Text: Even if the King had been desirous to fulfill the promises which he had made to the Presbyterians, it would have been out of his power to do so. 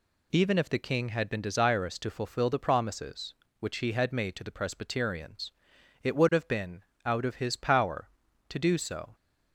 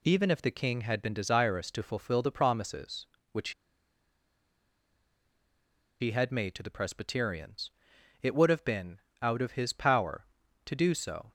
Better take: first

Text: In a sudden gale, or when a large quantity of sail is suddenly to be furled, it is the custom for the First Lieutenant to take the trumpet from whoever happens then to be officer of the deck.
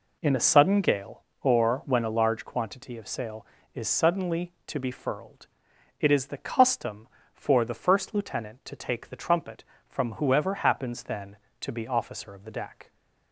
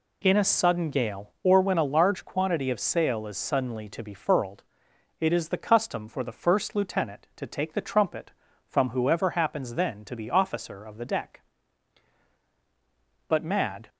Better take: first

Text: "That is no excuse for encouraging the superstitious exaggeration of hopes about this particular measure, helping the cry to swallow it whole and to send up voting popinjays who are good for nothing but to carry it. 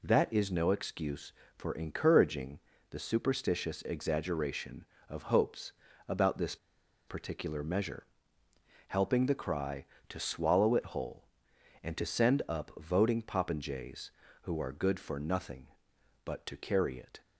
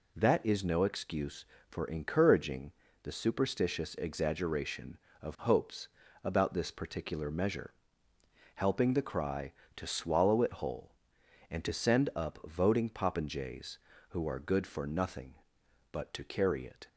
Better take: second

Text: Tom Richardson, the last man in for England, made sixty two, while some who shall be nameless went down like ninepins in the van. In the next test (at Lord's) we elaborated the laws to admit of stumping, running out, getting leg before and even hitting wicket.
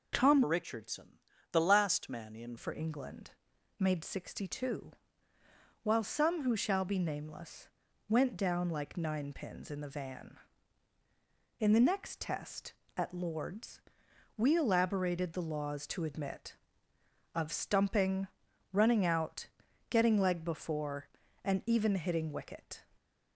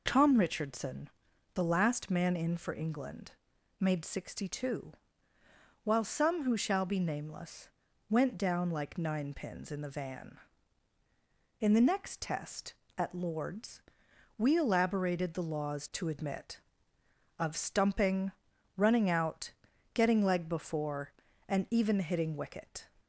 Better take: second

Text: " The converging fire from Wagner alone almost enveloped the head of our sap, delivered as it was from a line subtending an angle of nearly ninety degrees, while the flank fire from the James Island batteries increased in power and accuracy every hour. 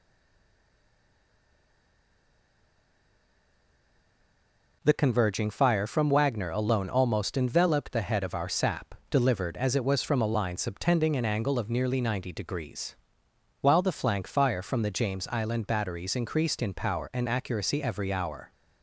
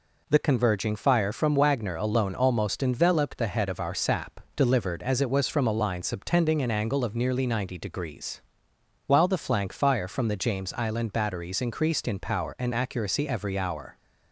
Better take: second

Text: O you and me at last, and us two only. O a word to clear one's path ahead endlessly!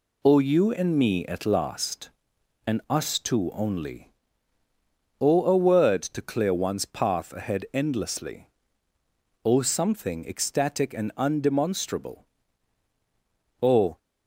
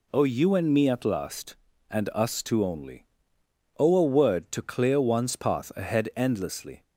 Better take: second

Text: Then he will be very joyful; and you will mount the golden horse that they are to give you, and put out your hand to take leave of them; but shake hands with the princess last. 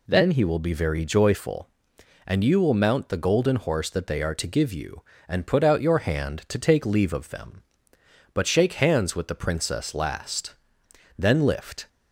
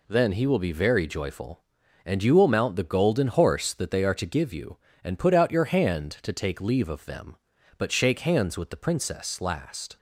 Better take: second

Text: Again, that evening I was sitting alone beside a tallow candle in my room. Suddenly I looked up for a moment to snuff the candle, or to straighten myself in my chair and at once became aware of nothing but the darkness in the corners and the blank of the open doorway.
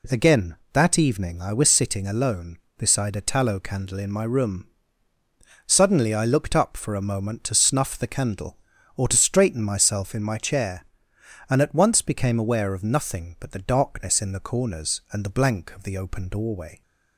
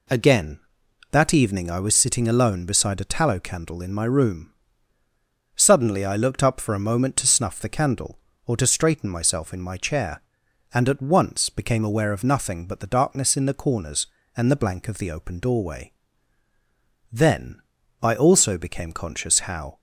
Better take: first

